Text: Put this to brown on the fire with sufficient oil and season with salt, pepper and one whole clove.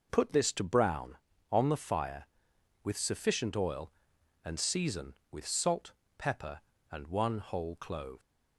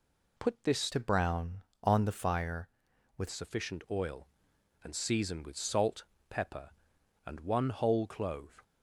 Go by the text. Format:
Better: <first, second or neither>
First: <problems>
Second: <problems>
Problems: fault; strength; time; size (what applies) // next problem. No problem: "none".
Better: first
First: none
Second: changes voice from "to" to "with"; from 0.9 to 3.2 s; 2.3 s long